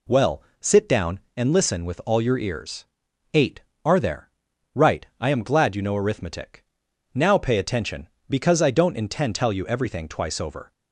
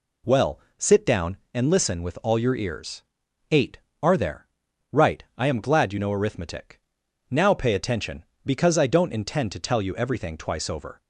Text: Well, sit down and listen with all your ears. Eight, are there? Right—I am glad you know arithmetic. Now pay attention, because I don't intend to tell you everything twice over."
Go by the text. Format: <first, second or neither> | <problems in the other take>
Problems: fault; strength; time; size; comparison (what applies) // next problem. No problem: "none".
second | skips "to"; at 9.3 s